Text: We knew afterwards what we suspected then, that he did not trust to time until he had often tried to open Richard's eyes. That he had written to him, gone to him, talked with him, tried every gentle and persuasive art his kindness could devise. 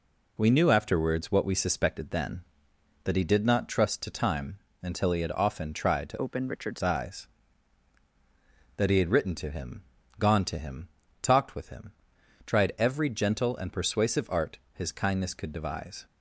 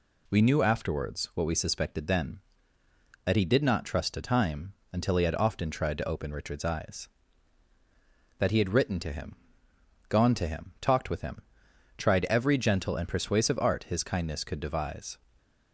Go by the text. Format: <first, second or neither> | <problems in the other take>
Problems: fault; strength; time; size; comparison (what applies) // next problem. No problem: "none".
second | pauses between "time" and "until"; slight; at 4.5 s; 0.24 s long; slight in the second // changes voice from "open" to "Richard's"; from 6.1 to 6.8 s; 0.7 s long // pauses between "art" and "his"; slight; at 14.5 s; 0.16 s long